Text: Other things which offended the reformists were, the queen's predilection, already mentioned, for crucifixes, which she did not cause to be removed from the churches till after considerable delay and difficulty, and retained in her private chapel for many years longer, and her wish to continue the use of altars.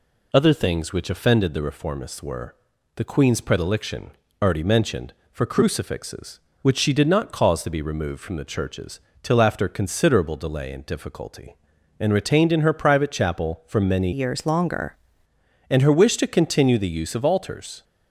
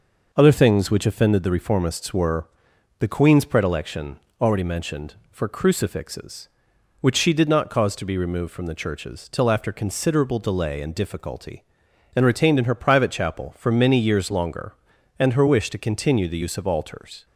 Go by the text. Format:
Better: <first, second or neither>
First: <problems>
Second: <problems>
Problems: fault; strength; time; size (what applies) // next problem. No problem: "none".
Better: second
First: pauses between "churches" and "till"; slight; at 9.0 s; 0.22 s long // changes voice from "years" to "longer"; from 14.1 to 14.9 s; 0.8 s long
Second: none